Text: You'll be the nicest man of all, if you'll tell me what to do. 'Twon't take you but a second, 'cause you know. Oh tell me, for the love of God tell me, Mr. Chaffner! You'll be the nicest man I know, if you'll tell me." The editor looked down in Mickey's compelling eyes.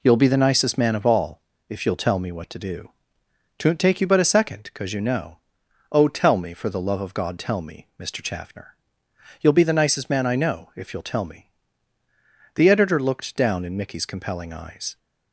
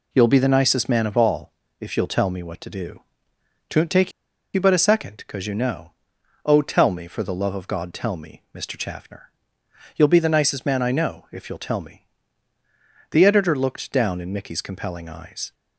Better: first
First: none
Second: pauses between "take" and "you"; at 4.1 s; 0.42 s long

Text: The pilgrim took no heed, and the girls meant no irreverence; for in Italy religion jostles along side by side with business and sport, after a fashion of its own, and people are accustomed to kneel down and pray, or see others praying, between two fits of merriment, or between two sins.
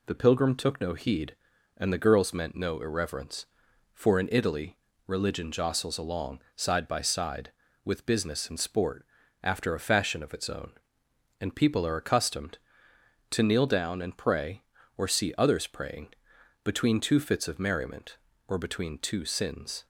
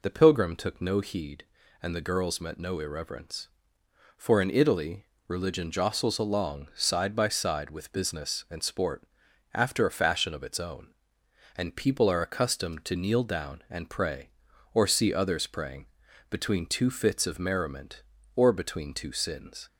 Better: first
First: pauses between "Italy" and "religion"; slight; at 4.7 s; 0.30 s long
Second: says "met" for "meant"; at 2.3 s // pauses between "Italy" and "religion"; slight; at 5.0 s; 0.22 s long

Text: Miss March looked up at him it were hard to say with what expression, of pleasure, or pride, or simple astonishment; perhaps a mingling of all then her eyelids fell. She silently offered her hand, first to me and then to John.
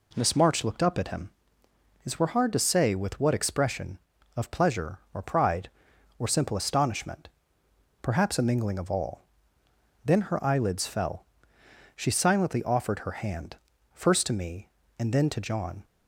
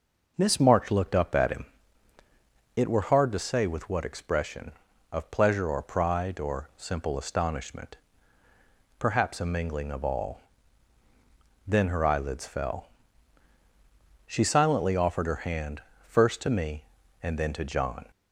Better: first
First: pauses between "him" and "it"; noticeable; at 1.2 s; 0.74 s long // pauses between "all" and "then"; noticeable; at 9.2 s; 0.80 s long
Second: changes voice at "March"; from 0.6 s on; 17.4 s long // pauses between "him" and "it"; at 1.6 s; 1.1 s long // pauses between "all" and "then"; at 10.4 s; 1.2 s long

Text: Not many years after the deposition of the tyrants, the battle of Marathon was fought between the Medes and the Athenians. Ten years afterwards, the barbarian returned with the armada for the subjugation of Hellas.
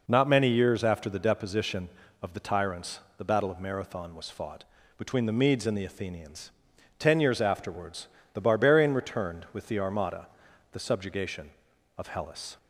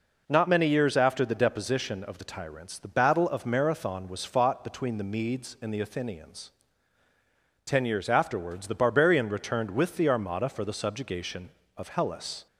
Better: second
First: pauses between "fought" and "between"; slight; at 4.6 s; 0.34 s long // skips "for"; at 10.4 s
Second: none

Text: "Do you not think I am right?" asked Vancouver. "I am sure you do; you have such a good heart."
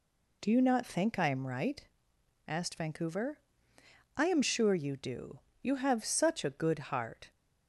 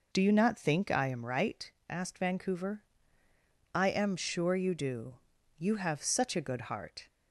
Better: neither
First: none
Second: none

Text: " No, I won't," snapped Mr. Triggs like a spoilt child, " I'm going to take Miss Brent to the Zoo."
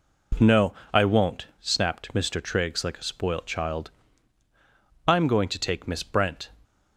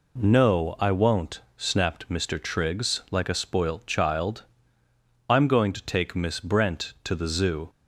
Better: second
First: stops before "to the Zoo"; at 6.6 s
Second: none

